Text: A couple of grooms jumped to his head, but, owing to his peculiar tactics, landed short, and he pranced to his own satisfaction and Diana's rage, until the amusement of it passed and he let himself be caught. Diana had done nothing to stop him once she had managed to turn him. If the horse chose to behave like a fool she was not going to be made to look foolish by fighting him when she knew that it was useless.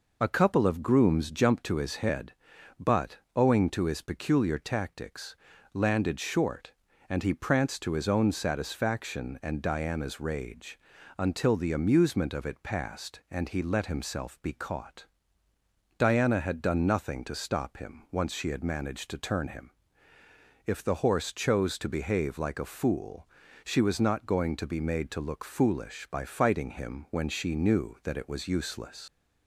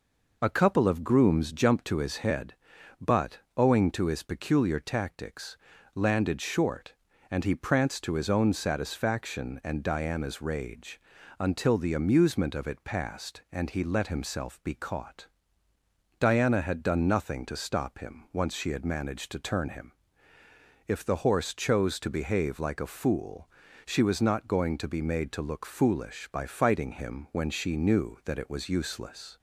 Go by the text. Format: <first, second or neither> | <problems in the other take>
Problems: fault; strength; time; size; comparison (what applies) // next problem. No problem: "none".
second | pauses between "fool" and "she"; at 23.2 s; 0.38 s long; also in the second // leaves "useless" unfinished; at 29.0 s; 90 ms